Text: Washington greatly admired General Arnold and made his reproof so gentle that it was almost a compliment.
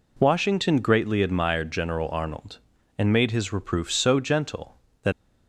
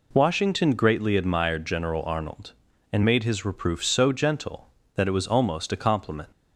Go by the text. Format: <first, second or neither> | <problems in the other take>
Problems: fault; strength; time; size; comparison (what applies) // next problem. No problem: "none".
second | stops before "it was almost a compliment"; at 5.1 s